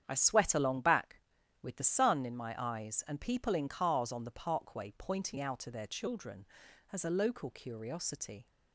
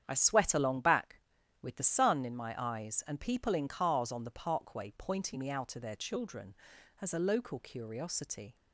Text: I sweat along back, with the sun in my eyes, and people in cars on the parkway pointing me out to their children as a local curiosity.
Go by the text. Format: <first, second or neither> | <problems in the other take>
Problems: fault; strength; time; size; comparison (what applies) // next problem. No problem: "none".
second | starts louder than the rest; strong; until 1.0 s; 9 dB; strong in the second // skips "me"; at 5.3 s